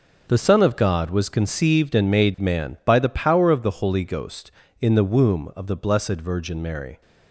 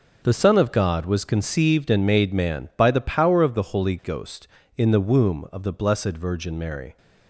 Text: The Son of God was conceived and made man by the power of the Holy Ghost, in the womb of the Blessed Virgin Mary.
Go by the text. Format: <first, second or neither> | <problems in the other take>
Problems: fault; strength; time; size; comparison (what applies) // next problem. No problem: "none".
neither | none